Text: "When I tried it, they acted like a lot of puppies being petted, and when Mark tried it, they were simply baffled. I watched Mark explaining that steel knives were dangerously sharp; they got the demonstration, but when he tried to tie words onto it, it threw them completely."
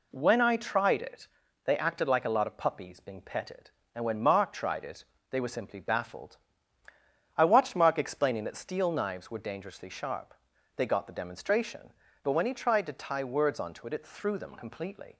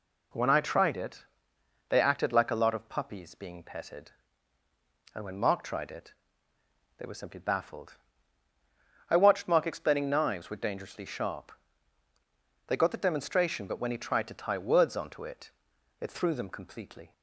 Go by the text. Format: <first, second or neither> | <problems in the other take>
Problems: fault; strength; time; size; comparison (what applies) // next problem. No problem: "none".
first | skips "that steel"; at 10.0 s